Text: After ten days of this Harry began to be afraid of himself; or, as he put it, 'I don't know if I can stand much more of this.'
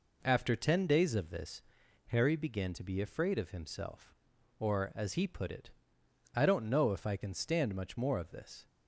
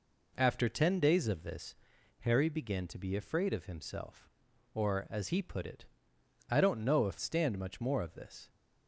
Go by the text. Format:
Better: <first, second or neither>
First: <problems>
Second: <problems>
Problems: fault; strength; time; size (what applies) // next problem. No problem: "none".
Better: first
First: pauses between "this" and "Harry"; noticeable; at 1.6 s; 0.46 s long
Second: pauses between "this" and "Harry"; noticeable; at 1.7 s; 0.46 s long // skips "I can"; at 7.1 s